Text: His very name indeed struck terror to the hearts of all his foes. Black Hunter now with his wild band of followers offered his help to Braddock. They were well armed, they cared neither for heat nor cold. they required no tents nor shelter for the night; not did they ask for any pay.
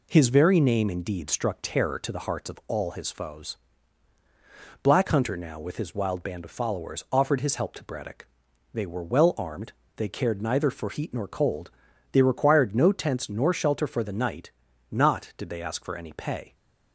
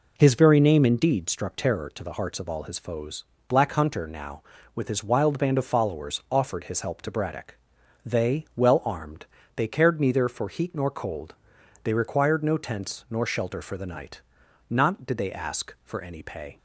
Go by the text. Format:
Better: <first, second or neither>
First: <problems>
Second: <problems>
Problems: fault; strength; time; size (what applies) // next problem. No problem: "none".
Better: first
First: none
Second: skips "were"; at 8.5 s